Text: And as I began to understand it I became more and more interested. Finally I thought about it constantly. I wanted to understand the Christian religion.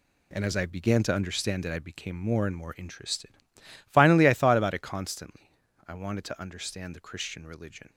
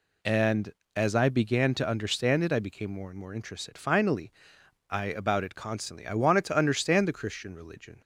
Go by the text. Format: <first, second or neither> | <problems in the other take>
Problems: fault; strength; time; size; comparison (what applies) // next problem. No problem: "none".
first | pauses between "Finally" and "I"; noticeable; at 4.3 s; 0.58 s long // skips "thought"; at 5.0 s